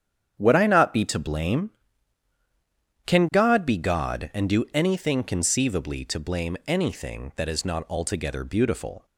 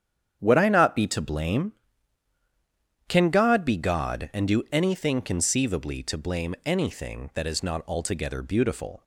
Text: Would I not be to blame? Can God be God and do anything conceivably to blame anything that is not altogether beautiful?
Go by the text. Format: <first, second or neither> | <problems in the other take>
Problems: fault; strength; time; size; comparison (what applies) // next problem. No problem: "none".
neither | starts louder than the rest; strong; the same in both